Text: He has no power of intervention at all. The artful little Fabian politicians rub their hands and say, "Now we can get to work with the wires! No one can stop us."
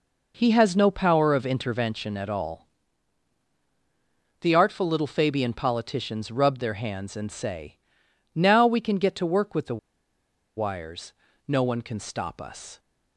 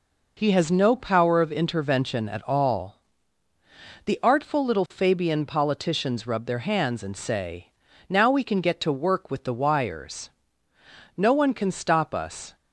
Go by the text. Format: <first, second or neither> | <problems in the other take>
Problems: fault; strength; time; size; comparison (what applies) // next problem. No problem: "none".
second | pauses between "the" and "wires"; noticeable; at 9.7 s; 0.79 s long